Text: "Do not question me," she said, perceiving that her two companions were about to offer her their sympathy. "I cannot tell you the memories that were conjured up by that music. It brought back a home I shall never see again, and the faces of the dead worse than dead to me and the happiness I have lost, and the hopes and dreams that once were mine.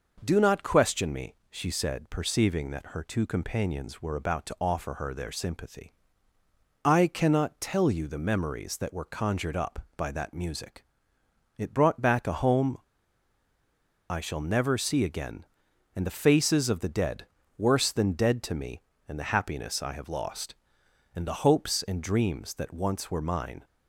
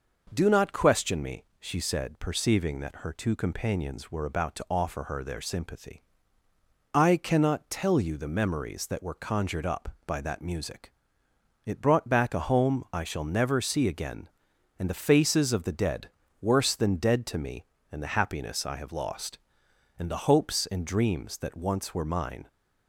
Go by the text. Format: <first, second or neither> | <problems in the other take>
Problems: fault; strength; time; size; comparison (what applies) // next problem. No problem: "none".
second | pauses between "home" and "I"; strong; at 12.7 s; 1.3 s long // pauses between "dead" and "worse"; slight; at 17.2 s; 0.32 s long; slight in the second